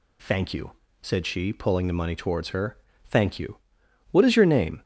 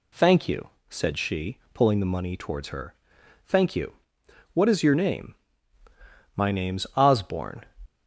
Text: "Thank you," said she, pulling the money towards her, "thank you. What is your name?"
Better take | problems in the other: first | goes on to say "My name's Osborne"; noticeable; from 6.3 s on; 1.2 s long

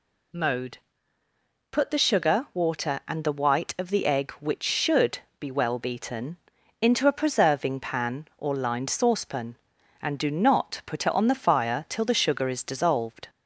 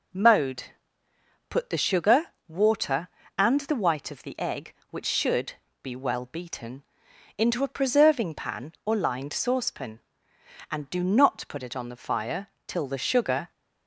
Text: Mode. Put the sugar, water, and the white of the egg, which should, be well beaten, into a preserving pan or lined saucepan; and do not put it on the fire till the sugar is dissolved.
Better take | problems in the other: first | pauses between "fire" and "till"; slight; at 12.4 s; 0.18 s long // stops before "is dissolved"; at 13.5 s

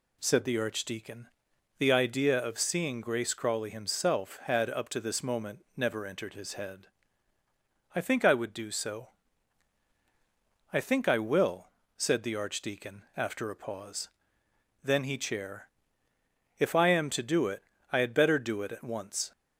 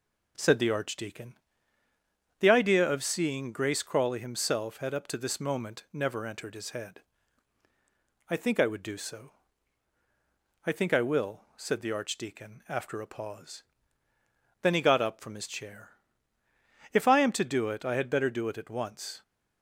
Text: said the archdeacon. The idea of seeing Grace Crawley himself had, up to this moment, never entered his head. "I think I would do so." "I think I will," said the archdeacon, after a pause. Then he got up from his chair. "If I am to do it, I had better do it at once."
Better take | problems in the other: second | skips "got up from his"; at 15.1 s

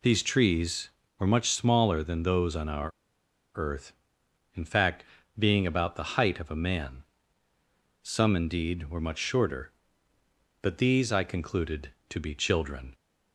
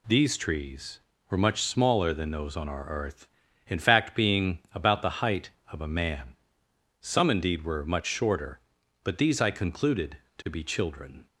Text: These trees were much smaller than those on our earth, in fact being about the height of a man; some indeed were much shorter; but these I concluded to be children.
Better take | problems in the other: second | pauses between "our" and "earth"; noticeable; at 2.9 s; 0.65 s long // pauses between "fact" and "being"; slight; at 5.0 s; 0.34 s long

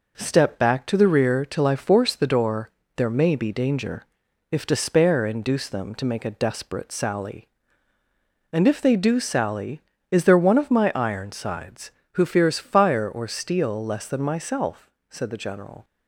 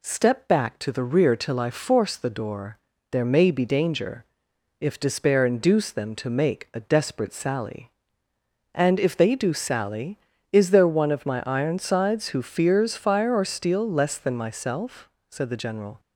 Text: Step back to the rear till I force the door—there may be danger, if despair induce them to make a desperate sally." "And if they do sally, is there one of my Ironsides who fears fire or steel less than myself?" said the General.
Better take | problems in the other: neither | none

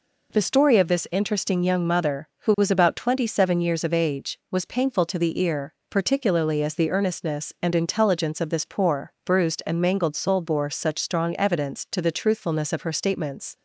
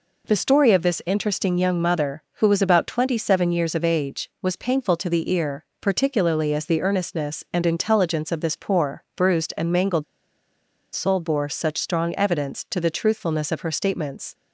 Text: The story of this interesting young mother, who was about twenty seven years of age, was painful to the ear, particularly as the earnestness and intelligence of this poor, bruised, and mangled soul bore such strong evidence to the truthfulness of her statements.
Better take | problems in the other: first | pauses between "mangled" and "soul"; noticeable; at 10.0 s; 0.90 s long

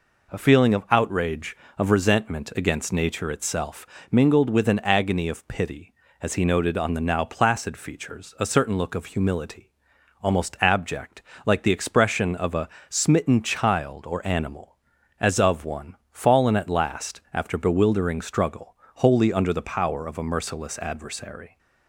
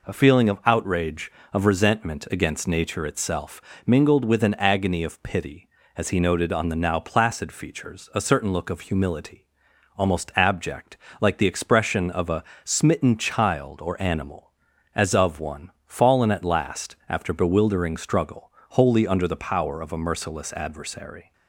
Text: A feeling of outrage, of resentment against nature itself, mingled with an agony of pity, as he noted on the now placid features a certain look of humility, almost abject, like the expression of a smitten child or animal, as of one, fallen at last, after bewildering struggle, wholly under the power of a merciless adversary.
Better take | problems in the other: neither | pauses between "a" and "smitten"; slight; the same in both

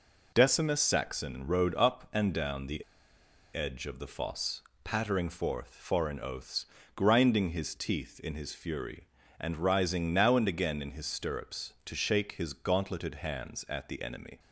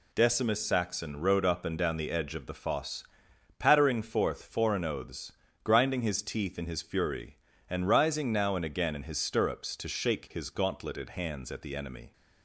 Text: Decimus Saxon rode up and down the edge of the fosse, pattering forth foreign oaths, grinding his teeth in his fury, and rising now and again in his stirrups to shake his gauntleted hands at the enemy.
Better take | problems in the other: second | pauses between "the" and "edge"; noticeable; at 2.8 s; 0.74 s long

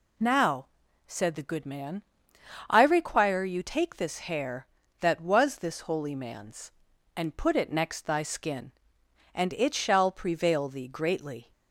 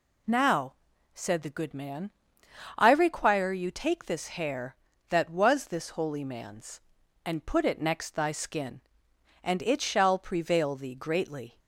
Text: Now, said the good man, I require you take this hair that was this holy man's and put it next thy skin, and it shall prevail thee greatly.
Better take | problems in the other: neither | none

